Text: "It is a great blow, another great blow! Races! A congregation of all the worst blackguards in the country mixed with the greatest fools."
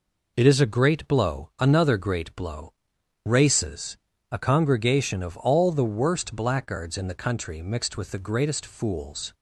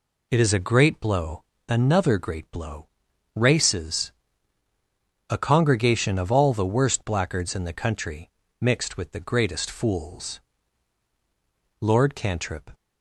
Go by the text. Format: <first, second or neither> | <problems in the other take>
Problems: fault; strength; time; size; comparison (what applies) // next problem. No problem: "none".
first | pauses between "country" and "mixed"; slight; at 8.2 s; 0.32 s long // goes on to say "Lord Cantrip"; noticeable; from 11.7 s on; 0.92 s long